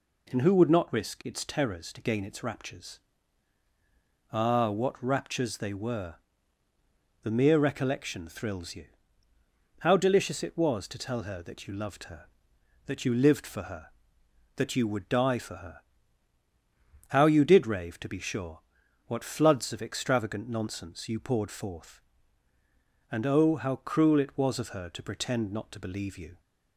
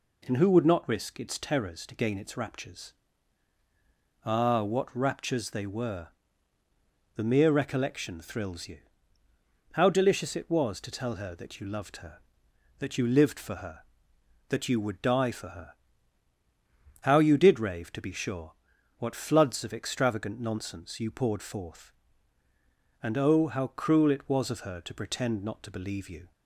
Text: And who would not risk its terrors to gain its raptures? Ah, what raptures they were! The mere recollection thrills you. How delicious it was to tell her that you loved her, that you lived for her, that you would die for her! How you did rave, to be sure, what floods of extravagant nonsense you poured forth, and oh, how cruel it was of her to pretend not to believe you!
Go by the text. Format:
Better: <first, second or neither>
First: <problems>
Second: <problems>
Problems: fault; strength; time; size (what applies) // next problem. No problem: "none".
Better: neither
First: none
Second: none